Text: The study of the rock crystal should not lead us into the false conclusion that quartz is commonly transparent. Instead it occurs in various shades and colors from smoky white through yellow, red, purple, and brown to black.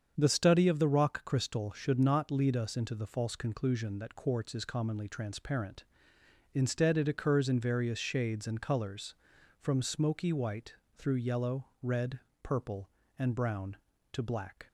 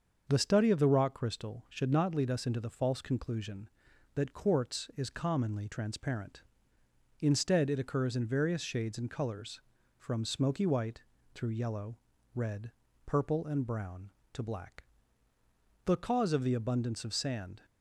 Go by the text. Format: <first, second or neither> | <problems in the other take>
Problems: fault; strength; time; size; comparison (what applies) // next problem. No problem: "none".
first | starts louder than the rest; until 1.2 s; 6.5 dB; strong in the first // pauses between "white" and "through"; slight; at 11.0 s; 0.30 s long; slight in the first // goes on to say "The cause of the abundance of sand"; strong; from 15.8 s on; 1.7 s long